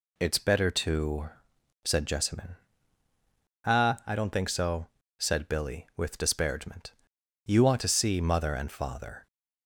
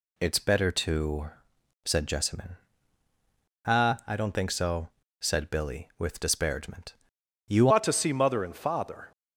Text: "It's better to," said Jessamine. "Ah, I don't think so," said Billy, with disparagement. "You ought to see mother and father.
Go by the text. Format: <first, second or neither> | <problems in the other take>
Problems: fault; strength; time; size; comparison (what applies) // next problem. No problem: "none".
first | changes voice at "ought"; from 7.6 s on; 1.5 s long